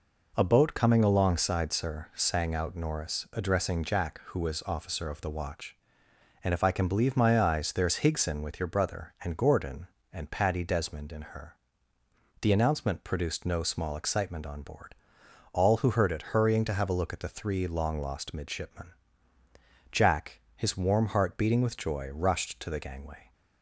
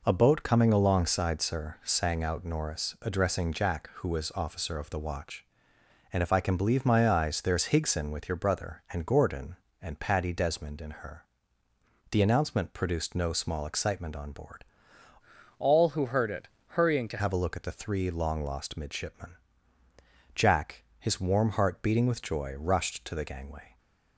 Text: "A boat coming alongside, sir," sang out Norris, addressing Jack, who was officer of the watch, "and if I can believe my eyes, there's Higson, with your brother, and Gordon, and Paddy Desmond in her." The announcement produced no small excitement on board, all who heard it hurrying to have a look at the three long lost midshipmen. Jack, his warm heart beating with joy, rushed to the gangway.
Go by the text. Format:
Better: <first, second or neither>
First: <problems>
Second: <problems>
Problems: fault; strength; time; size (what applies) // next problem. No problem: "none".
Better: first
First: none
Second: changes voice from "all" to "to"; from 15.5 to 17.1 s; 1.6 s long // pauses between "it" and "hurrying"; slight; at 16.4 s; 0.20 s long